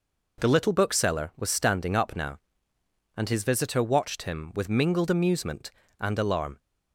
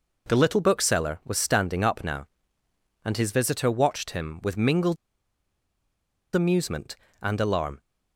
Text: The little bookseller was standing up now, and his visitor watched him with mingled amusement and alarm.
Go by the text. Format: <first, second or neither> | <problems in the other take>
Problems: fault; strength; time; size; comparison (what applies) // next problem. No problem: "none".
first | pauses between "mingled" and "amusement"; strong; at 4.9 s; 1.4 s long